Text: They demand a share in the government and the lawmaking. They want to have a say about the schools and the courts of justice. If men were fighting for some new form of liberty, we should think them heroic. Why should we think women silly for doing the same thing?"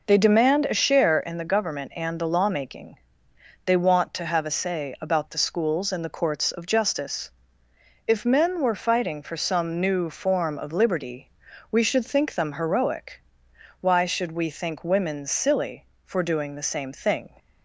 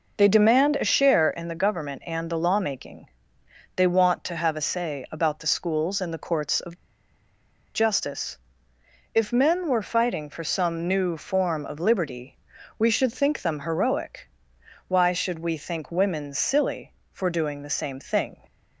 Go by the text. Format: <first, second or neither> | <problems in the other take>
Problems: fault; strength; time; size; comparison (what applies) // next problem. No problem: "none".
first | pauses between "of" and "justice"; at 6.7 s; 1.0 s long